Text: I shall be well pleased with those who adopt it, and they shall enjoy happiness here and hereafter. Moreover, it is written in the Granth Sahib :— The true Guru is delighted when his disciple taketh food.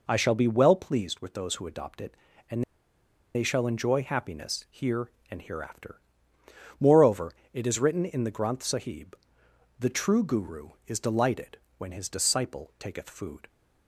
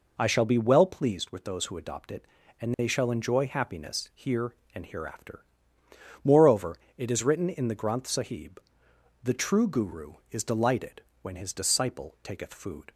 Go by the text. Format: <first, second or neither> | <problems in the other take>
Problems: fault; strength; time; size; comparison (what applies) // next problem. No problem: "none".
second | pauses between "and" and "they"; noticeable; at 2.6 s; 0.71 s long // pauses between "delighted" and "when"; slight; at 11.5 s; 0.18 s long; slight in the second